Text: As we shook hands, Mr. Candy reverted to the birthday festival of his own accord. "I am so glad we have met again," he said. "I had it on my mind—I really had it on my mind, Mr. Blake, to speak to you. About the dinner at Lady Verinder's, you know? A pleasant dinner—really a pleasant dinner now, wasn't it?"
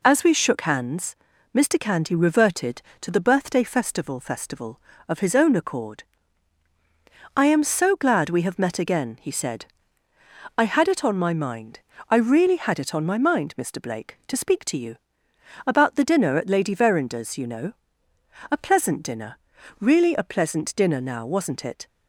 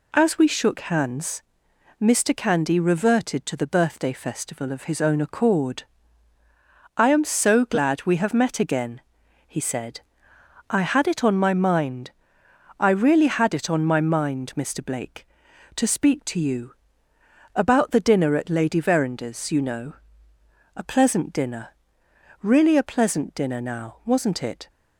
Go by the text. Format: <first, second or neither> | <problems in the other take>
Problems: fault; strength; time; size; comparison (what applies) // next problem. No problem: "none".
second | says "festival" twice; at 4.1 s